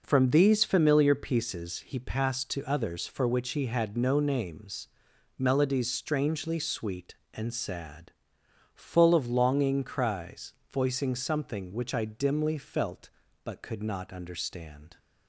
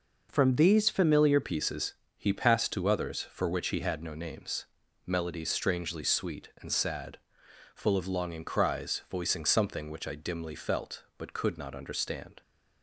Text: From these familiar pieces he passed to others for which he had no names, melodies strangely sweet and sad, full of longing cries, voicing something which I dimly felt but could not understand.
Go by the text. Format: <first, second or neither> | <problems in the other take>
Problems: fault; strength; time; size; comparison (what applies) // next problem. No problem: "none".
first | changes voice at "pieces"; from 1.4 s on; 11.0 s long // pauses between "pieces" and "he"; slight; at 1.9 s; 0.24 s long